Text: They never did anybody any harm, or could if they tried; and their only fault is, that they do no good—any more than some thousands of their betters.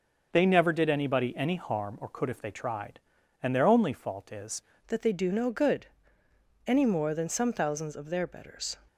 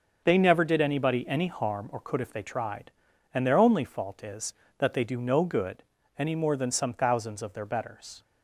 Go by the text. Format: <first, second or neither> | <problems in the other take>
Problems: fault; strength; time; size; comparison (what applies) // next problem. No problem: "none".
second | starts louder than the rest; until 1.3 s; 6 dB; also in the second // changes voice at "that"; from 4.8 s on; 3.9 s long